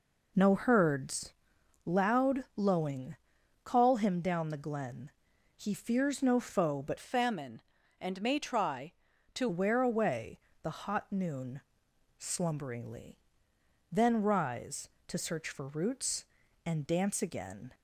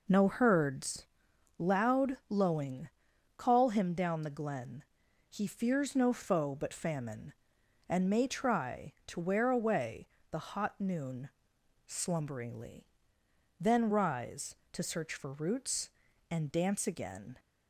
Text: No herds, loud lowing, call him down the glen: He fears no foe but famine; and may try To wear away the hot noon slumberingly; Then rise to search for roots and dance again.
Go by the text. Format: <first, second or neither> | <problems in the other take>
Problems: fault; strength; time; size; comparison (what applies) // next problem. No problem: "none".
second | changes voice from "famine" to "To"; from 6.9 to 9.4 s; 2.5 s long // pauses between "away" and "the"; slight; at 10.3 s; 0.24 s long; slight in the second // pauses between "noon" and "slumberingly"; noticeable; at 11.5 s; 0.60 s long; noticeable in the second